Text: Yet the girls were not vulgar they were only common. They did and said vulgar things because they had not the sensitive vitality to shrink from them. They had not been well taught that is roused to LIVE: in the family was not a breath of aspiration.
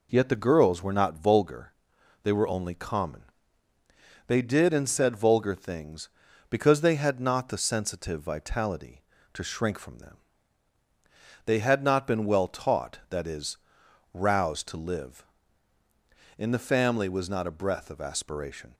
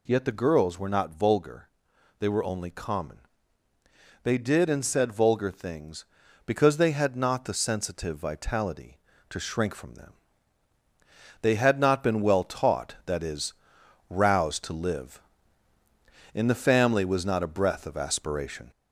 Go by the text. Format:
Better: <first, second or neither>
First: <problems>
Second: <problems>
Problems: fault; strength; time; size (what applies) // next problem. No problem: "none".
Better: first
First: pauses between "vulgar" and "they"; noticeable; at 1.7 s; 0.50 s long // pauses between "is" and "roused"; noticeable; at 13.5 s; 0.56 s long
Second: gets louder; slight; throughout; 2.5 dB // pauses between "vulgar" and "they"; noticeable; at 1.6 s; 0.50 s long // pauses between "is" and "roused"; noticeable; at 13.5 s; 0.56 s long